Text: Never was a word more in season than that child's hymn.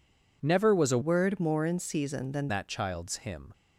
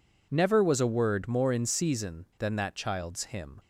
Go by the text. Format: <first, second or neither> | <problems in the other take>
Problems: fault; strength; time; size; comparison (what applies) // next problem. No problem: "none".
second | changes voice from "word" to "than"; from 1.0 to 2.4 s; 1.4 s long